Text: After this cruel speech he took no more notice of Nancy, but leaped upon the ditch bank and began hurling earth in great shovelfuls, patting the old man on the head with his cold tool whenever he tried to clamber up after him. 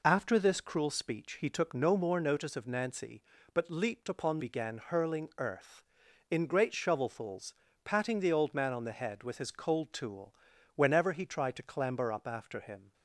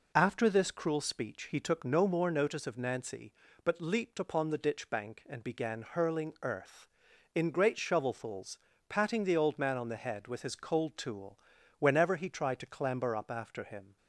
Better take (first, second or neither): second